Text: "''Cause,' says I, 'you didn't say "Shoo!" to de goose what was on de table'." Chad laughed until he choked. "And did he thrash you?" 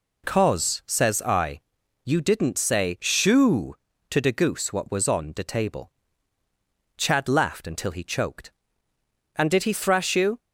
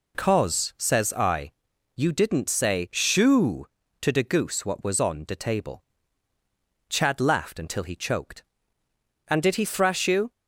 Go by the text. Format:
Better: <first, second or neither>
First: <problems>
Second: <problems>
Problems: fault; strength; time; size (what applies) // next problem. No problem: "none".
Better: neither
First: none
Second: none